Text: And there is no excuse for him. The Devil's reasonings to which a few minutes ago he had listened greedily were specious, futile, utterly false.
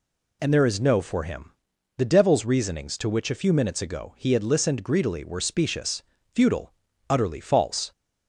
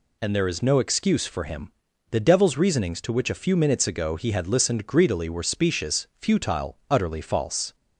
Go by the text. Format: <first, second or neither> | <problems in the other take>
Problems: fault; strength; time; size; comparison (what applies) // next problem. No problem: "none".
second | skips "excuse"; at 1.0 s